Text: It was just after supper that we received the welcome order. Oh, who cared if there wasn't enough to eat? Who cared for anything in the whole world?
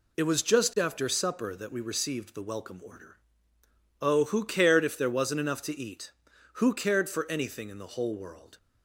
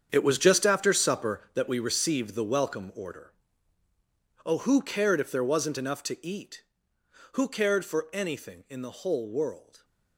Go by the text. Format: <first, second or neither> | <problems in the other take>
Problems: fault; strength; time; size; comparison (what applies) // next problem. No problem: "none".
first | gets quieter; strong; throughout; 13.5 dB